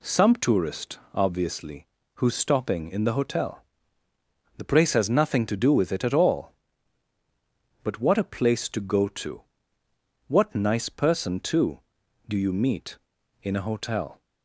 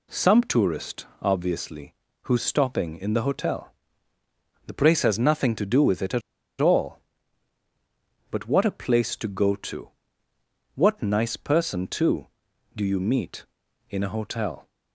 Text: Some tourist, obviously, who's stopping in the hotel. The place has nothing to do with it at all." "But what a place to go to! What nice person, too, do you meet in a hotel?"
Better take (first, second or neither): first